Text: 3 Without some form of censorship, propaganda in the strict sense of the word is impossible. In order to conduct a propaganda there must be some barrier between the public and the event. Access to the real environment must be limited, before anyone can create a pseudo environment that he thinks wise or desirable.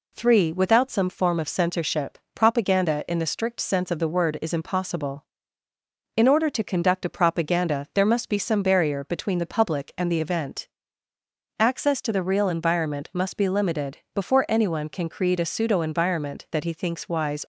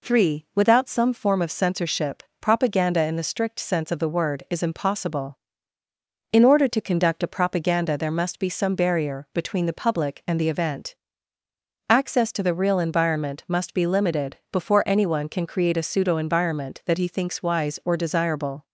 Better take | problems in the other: second | stops before "or desirable"; at 17.4 s

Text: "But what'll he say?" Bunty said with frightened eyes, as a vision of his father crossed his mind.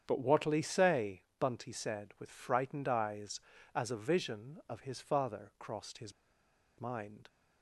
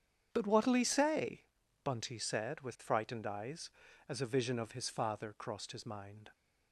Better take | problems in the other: second | starts louder than the rest; strong; until 1.0 s; 8 dB; strong in the second // pauses between "his" and "mind"; noticeable; at 6.1 s; 0.66 s long

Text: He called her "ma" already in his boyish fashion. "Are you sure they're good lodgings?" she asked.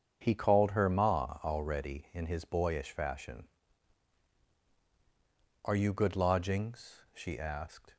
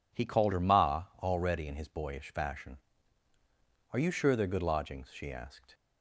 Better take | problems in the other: second | starts louder than the rest; strong; until 1.2 s; 7.5 dB // skips "sure they're"; at 5.9 s

